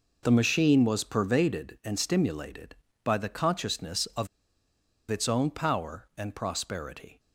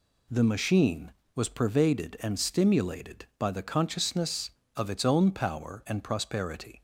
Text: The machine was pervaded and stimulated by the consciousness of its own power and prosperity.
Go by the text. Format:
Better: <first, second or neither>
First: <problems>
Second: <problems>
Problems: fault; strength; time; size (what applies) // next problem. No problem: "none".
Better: second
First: pauses between "of" and "its"; noticeable; at 4.2 s; 0.83 s long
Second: none